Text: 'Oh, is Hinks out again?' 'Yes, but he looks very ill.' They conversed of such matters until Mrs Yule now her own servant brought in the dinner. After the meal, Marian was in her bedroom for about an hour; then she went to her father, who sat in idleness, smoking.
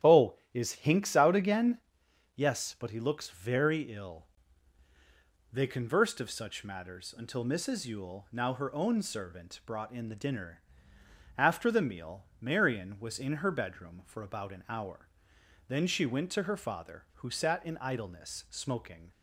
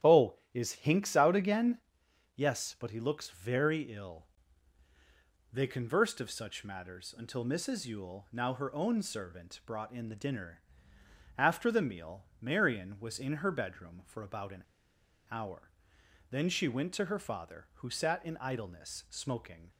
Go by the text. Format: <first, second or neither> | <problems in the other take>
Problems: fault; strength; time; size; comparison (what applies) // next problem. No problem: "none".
first | starts louder than the rest; strong; until 1.2 s; 11.5 dB; strong in the first // pauses between "an" and "hour"; noticeable; at 14.6 s; 0.66 s long